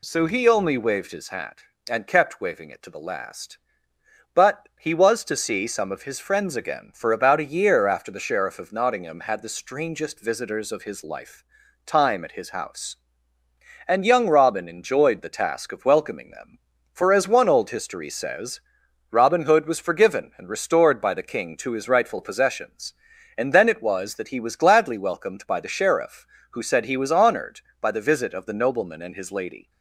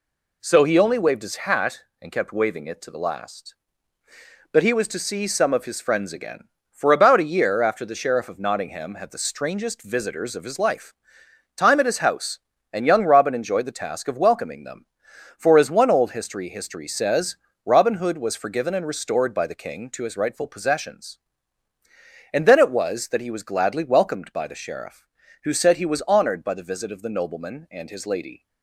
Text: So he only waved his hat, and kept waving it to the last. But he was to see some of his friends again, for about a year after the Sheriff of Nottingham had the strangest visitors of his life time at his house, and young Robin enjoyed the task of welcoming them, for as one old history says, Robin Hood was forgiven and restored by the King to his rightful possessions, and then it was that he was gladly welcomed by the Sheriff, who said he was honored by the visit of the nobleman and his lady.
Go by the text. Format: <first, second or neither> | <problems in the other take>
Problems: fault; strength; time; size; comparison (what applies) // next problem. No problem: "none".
first | pauses between "life" and "time"; noticeable; at 10.9 s; 0.64 s long; also in the first // says "history" twice; at 16.4 s